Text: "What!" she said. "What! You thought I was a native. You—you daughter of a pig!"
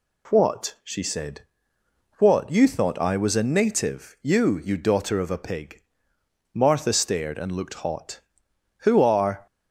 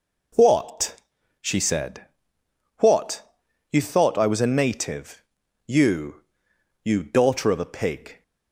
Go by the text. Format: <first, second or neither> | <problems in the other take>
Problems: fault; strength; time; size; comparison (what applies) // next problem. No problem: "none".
second | goes on to say "Martha stared and looked hot Who are"; strong; from 6.5 s on; 2.9 s long